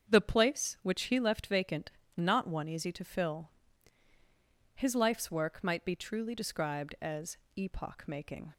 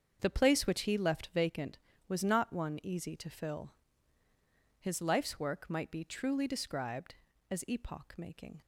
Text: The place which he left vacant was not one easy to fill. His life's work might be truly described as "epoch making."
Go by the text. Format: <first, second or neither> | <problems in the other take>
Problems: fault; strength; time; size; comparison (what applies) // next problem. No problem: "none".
second | starts louder than the rest; strong; until 1.1 s; 7 dB; also in the second // skips "was"; at 2.0 s // pauses between "as" and "epoch"; slight; at 7.3 s; 0.20 s long